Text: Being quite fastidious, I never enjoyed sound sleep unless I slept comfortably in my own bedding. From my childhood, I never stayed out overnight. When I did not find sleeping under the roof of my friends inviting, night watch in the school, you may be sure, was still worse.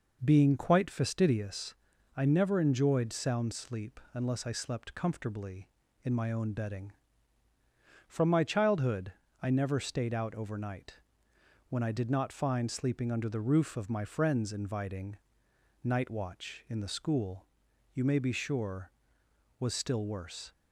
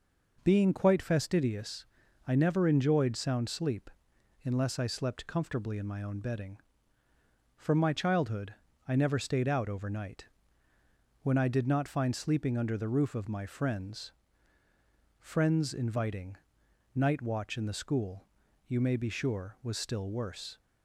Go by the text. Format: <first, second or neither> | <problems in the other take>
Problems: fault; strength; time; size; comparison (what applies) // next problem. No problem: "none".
first | pauses between "sleep" and "unless"; noticeable; at 3.8 s; 0.56 s long // says "friends" twice; at 15.1 s